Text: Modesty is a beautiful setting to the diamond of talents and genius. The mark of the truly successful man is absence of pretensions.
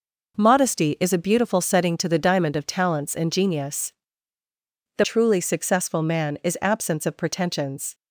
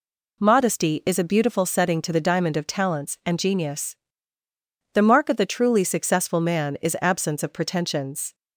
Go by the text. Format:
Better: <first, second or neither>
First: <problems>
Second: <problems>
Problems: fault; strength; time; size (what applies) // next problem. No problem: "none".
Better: second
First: skips "mark of the"; at 5.0 s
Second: none